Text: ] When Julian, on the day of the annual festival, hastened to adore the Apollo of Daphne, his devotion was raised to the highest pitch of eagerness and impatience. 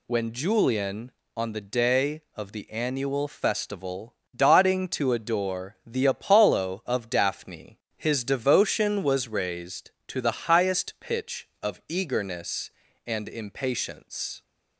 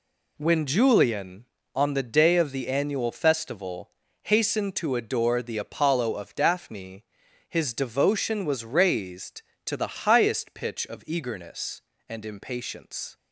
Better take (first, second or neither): second